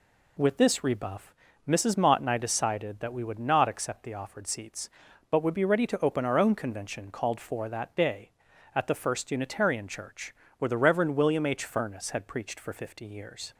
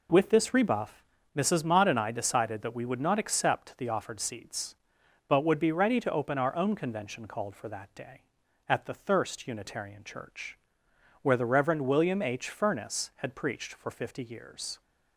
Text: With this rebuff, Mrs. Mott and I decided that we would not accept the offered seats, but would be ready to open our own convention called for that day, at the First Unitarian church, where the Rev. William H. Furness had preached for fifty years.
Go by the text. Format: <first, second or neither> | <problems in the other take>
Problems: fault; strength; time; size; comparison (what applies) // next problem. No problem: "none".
first | says "Thirst" for "First"; at 8.9 s